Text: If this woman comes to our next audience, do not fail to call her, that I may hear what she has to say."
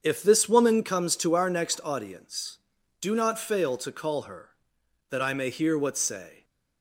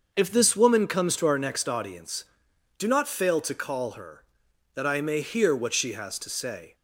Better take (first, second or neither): second